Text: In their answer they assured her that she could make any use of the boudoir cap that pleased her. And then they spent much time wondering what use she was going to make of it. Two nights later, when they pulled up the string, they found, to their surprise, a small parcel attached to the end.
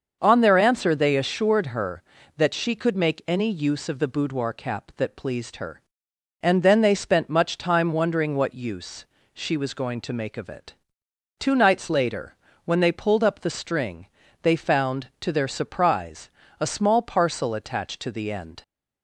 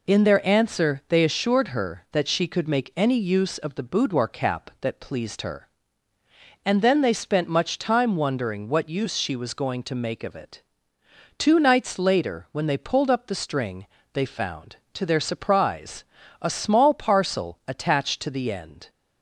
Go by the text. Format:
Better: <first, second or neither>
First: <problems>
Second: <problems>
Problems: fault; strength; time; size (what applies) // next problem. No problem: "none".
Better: second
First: starts louder than the rest; until 1.2 s; 6.5 dB // says "On" for "In"; at 0.2 s // pauses between "use" and "she"; slight; at 9.0 s; 0.30 s long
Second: none